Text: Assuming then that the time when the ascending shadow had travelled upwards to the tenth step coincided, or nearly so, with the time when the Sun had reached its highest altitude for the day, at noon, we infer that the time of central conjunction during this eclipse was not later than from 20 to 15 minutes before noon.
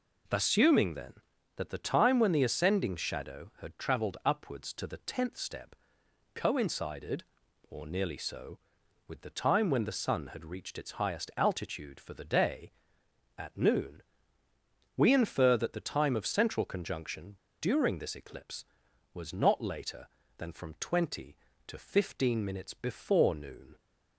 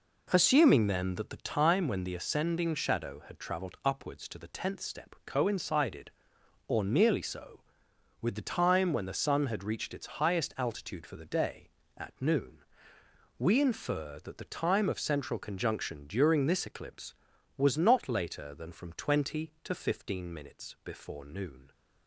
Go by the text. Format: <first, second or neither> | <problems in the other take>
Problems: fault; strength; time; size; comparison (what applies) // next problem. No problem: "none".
second | pauses between "step" and "coincided"; noticeable; at 5.7 s; 0.60 s long // pauses between "conjunction" and "during"; slight; at 17.3 s; 0.24 s long